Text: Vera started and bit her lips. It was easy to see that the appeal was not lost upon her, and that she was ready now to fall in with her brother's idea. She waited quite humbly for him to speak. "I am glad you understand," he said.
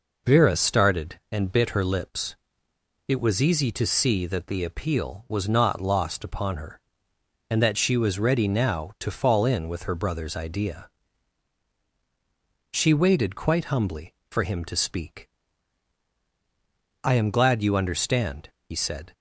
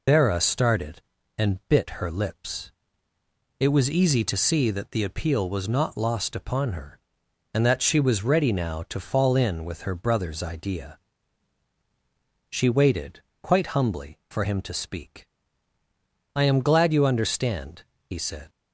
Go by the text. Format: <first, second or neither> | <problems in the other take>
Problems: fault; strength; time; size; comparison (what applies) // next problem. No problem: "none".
first | loses the start of "Vera"; at 0.0 s; 105 ms // pauses between "waited" and "quite"; slight; at 13.2 s; 0.20 s long